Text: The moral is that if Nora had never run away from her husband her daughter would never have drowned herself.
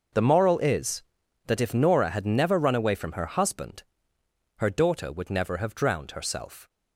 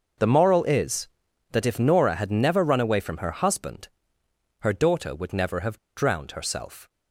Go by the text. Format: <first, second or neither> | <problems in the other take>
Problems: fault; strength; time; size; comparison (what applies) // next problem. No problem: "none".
first | starts louder than the rest; noticeable; until 1.6 s; 6 dB; noticeable in the first // pauses between "husband" and "her"; noticeable; at 3.8 s; 0.72 s long; noticeable in the first // pauses between "have" and "drowned"; slight; at 5.7 s; 0.20 s long